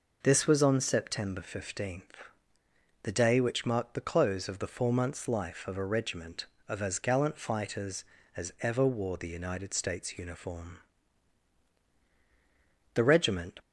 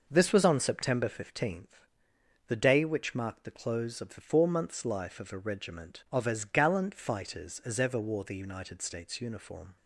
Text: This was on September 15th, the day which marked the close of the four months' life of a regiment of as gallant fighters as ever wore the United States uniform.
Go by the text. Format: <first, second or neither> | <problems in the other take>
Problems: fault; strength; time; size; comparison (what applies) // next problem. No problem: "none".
second | goes on to say "The regiment"; noticeable; from 12.9 s on; 0.66 s long